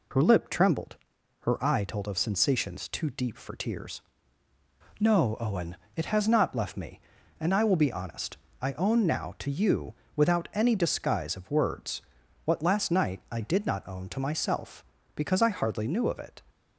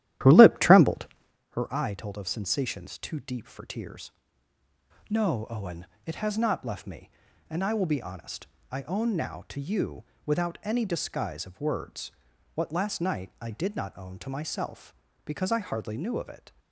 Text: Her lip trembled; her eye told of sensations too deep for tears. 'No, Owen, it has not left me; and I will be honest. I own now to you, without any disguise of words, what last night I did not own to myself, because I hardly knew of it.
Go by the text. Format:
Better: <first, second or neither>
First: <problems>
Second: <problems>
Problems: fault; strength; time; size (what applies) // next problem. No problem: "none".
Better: first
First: none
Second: starts louder than the rest; strong; until 1.4 s; 13 dB